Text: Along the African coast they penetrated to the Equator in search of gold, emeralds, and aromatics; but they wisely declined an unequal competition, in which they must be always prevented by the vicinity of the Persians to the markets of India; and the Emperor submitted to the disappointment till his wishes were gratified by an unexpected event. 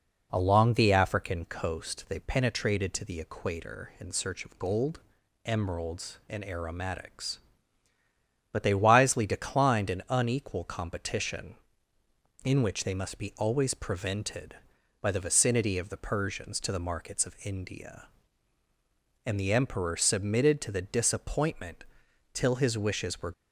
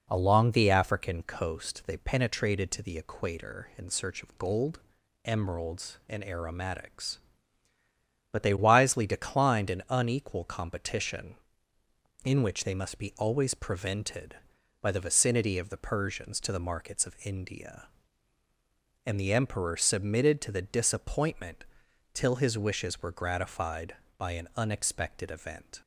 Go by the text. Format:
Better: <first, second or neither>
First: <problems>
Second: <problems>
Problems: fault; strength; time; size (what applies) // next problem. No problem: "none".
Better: second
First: pauses between "disappointment" and "till"; noticeable; at 21.8 s; 0.50 s long // stops before "gratified by an unexpected event"; at 23.3 s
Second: pauses between "disappointment" and "till"; noticeable; at 21.6 s; 0.50 s long